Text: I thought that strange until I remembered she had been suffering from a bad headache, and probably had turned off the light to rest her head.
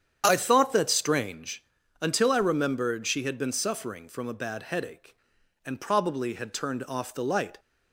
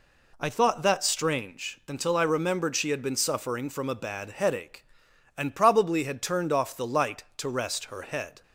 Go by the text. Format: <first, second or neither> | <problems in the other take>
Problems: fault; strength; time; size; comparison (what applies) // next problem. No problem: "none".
second | starts louder than the rest; strong; until 1.2 s; 9 dB // pauses between "strange" and "until"; at 1.6 s; 0.38 s long // stops before "to rest her head"; at 7.5 s